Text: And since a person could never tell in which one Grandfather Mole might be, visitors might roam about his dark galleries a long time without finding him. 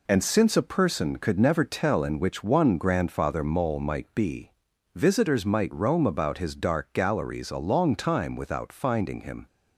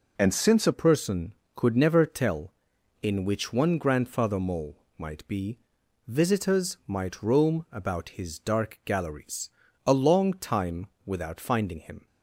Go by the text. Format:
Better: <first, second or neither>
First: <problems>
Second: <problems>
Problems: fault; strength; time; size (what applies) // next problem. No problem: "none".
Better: first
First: none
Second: changes voice at "person"; from 0.7 s on; 11.3 s long // pauses between "Mole" and "might"; slight; at 4.7 s; 0.22 s long // pauses between "galleries" and "a"; slight; at 9.4 s; 0.36 s long // pauses between "time" and "without"; slight; at 10.8 s; 0.18 s long